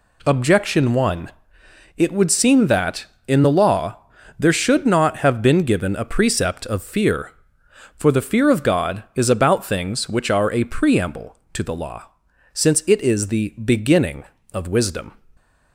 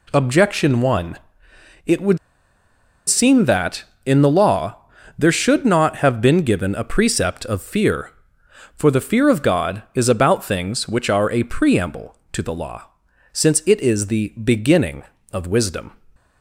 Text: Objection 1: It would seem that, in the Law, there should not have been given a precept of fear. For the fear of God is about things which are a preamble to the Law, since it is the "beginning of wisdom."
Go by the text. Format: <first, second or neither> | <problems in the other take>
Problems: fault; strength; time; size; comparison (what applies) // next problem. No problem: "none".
first | pauses between "would" and "seem"; noticeable; at 2.1 s; 0.89 s long